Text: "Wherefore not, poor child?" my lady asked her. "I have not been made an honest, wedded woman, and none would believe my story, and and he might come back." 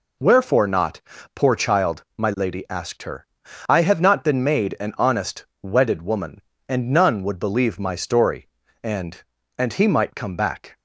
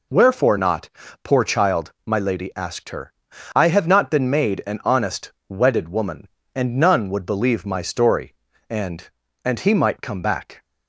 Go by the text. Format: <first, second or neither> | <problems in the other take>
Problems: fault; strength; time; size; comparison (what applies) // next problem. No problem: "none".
neither | none